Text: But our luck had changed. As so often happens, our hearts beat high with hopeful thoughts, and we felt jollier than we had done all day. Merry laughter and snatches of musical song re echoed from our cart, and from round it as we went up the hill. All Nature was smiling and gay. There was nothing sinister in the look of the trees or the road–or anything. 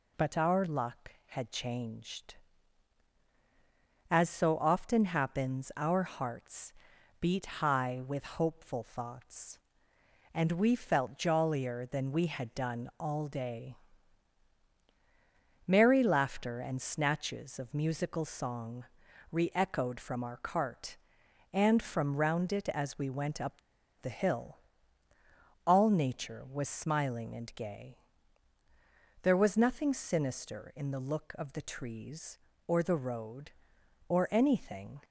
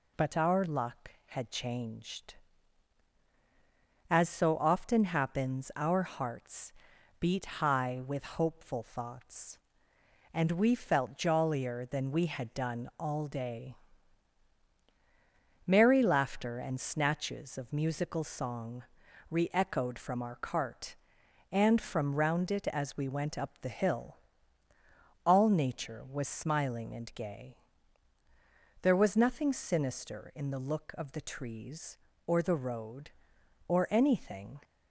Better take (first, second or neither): second